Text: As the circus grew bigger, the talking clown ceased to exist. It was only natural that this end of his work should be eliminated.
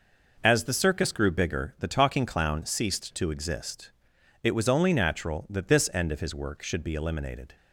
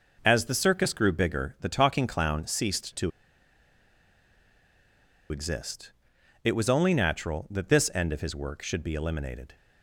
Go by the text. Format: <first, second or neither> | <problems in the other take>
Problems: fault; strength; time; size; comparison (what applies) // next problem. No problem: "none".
first | pauses between "to" and "exist"; strong; at 3.0 s; 2.2 s long